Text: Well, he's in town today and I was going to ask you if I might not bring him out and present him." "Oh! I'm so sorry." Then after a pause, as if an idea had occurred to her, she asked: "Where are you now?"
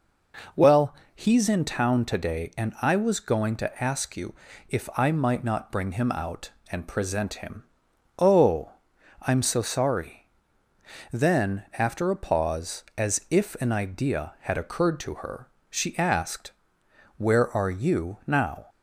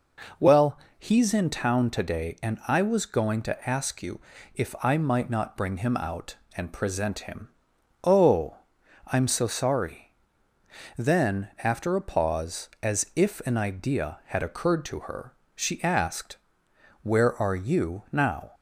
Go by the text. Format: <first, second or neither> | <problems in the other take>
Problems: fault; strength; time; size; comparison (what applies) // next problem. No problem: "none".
neither | pauses between "you" and "if"; slight; the same in both